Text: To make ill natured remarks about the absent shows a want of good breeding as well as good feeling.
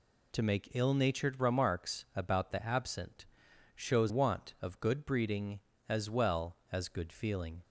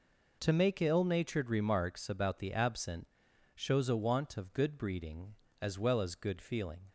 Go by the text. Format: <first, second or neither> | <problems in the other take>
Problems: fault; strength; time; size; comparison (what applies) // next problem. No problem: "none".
second | pauses between "absent" and "shows"; noticeable; at 3.2 s; 0.50 s long; noticeable in the second // skips "a"; at 4.0 s